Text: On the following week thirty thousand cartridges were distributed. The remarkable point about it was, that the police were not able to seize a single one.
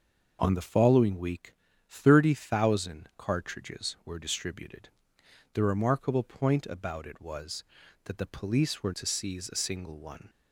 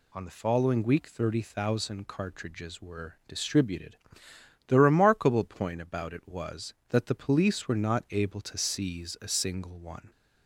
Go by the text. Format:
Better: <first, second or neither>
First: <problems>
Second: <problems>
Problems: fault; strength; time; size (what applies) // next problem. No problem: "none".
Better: second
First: starts louder than the rest; until 1.4 s; 6 dB // pauses between "week" and "thirty"; slight; at 1.5 s; 0.34 s long // skips "not able"; at 8.9 s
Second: none